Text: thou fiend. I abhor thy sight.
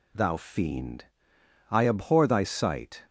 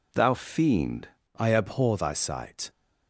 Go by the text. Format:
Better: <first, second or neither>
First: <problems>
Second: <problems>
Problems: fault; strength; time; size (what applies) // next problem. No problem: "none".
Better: first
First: none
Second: changes voice at "I"; from 1.3 s on; 1.3 s long